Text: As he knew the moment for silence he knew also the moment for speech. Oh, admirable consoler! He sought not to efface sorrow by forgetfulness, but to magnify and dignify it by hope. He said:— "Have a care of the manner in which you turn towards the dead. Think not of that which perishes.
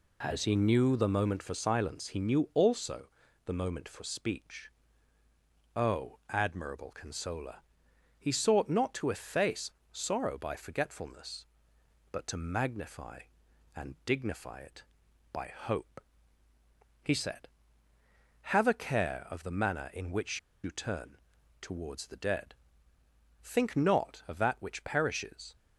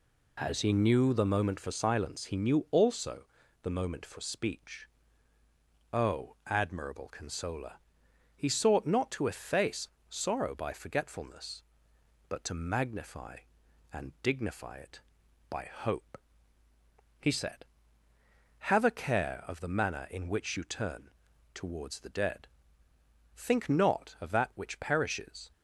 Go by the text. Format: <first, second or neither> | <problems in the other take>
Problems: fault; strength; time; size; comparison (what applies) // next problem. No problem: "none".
second | pauses between "also" and "the"; at 3.0 s; 0.38 s long; also in the second // pauses between "efface" and "sorrow"; slight; at 9.7 s; 0.20 s long; slight in the second // pauses between "which" and "you"; slight; at 20.3 s; 0.24 s long // pauses between "turn" and "towards"; at 21.1 s; 0.42 s long; also in the second